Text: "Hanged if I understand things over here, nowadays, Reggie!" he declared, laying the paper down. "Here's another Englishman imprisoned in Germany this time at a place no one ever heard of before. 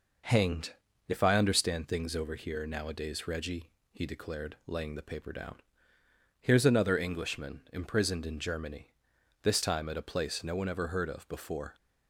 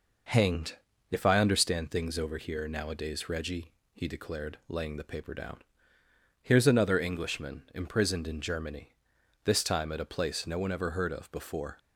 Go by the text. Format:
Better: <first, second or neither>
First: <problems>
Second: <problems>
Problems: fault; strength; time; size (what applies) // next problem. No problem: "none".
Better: neither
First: pauses between "Hanged" and "if"; slight; at 0.7 s; 0.34 s long // pauses between "Germany" and "this"; noticeable; at 8.9 s; 0.48 s long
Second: pauses between "Hanged" and "if"; slight; at 0.7 s; 0.34 s long // pauses between "Germany" and "this"; noticeable; at 8.9 s; 0.48 s long